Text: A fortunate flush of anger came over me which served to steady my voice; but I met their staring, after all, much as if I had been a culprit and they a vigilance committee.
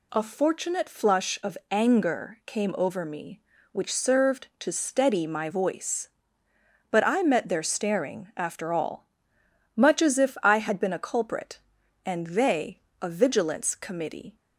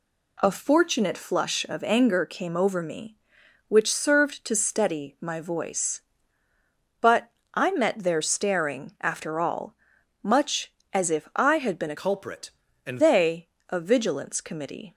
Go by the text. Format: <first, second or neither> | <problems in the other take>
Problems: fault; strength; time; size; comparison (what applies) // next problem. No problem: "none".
first | pauses between "but" and "I"; slight; at 7.3 s; 0.24 s long // changes voice from "culprit" to "and"; from 11.9 to 12.9 s; 1.0 s long // pauses between "they" and "a"; slight; at 13.4 s; 0.20 s long; slight in the first